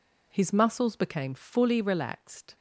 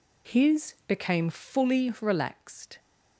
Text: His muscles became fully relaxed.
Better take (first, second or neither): first